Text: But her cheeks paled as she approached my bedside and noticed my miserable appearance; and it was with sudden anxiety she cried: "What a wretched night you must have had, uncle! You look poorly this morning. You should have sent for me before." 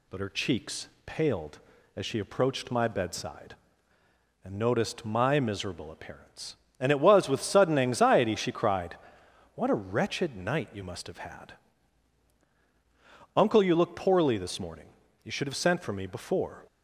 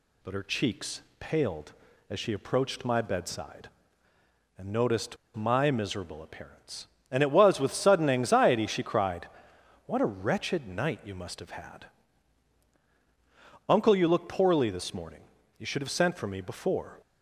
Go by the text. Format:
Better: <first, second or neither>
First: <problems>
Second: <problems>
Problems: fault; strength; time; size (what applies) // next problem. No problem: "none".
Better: first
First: pauses between "cheeks" and "paled"; slight; at 0.8 s; 0.18 s long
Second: pauses between "cheeks" and "paled"; slight; at 1.0 s; 0.18 s long // pauses between "noticed" and "my"; slight; at 5.1 s; 0.20 s long